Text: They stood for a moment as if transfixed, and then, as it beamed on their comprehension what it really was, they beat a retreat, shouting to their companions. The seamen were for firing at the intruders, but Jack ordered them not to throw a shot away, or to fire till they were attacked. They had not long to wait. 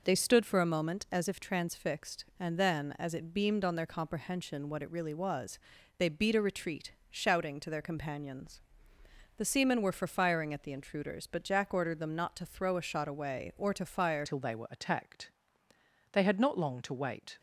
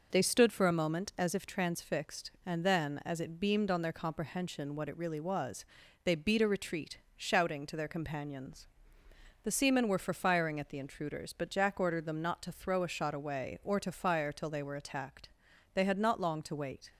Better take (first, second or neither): second